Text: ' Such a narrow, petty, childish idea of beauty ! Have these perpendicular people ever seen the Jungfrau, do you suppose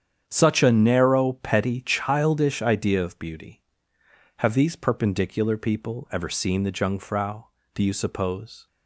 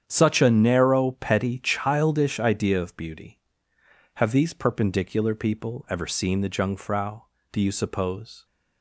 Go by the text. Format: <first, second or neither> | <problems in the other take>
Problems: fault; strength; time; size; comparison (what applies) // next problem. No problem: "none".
neither | starts louder than the rest; strong; the same in both